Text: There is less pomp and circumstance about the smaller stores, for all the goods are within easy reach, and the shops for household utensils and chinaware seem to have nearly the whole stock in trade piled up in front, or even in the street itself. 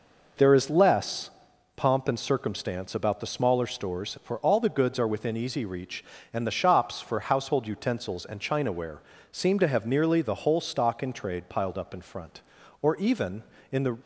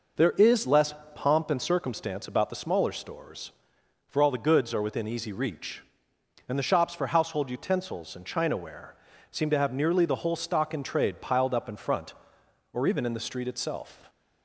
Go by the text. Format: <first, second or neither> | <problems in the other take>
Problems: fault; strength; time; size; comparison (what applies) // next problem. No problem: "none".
second | pauses between "less" and "pomp"; noticeable; at 1.2 s; 0.46 s long; slight in the second // pauses between "chinaware" and "seem"; slight; at 8.9 s; 0.30 s long; slight in the second // stops before "street itself"; at 14.0 s